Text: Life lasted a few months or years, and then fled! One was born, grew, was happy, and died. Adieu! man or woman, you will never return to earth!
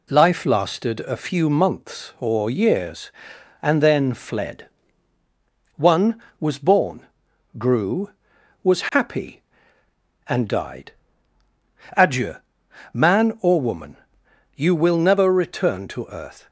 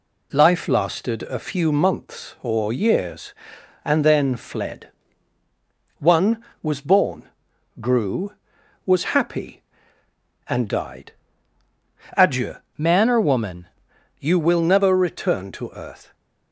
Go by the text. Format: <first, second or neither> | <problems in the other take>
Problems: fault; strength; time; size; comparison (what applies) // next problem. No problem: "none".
first | changes voice from "man" to "woman"; from 12.7 to 13.6 s; 0.9 s long